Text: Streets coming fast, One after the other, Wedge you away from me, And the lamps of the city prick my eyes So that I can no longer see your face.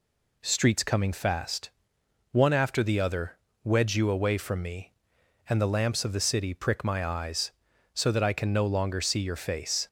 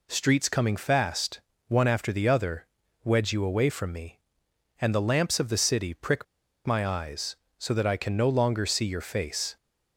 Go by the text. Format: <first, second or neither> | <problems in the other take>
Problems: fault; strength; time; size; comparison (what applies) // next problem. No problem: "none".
first | pauses between "prick" and "my"; at 6.2 s; 0.41 s long